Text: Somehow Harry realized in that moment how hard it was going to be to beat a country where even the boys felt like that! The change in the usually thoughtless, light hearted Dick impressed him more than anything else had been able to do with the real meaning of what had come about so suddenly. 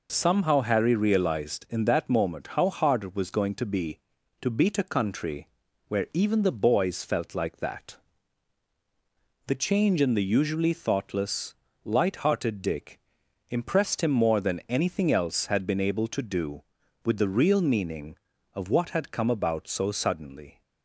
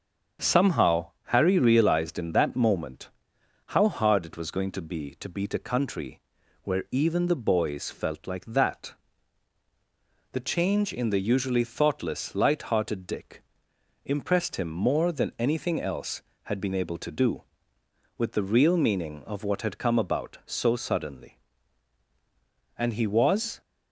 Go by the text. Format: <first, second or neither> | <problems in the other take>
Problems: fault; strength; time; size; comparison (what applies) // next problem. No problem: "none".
first | starts louder than the rest; until 1.5 s; 7 dB // pauses between "moment" and "how"; noticeable; at 3.1 s; 0.56 s long // pauses between "country" and "where"; at 6.2 s; 0.40 s long; also in the first // pauses between "Dick" and "impressed"; noticeable; at 13.4 s; 0.60 s long; noticeable in the first // goes on to say "And he was"; noticeable; from 22.7 s on; 0.82 s long